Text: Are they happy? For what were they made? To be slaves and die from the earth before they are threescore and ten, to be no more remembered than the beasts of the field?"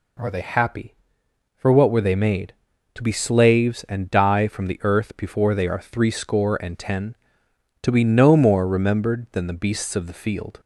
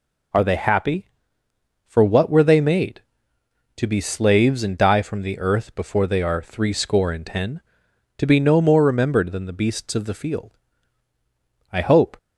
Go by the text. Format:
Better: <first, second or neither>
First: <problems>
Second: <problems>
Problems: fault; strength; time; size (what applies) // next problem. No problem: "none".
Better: first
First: none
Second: goes on to say "I hope"; slight; from 11.7 s on; 0.44 s long